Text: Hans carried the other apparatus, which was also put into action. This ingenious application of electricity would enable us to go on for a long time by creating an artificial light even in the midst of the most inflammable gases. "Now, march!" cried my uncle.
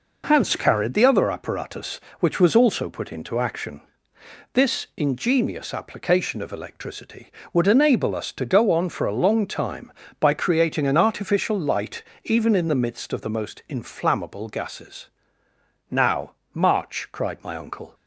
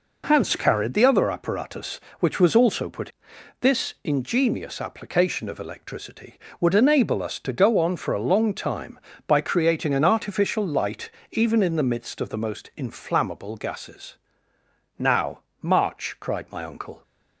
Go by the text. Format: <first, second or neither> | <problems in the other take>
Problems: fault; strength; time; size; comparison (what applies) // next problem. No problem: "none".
first | skips "into action"; at 3.3 s // pauses between "light" and "even"; slight; at 11.0 s; 0.22 s long; slight in the first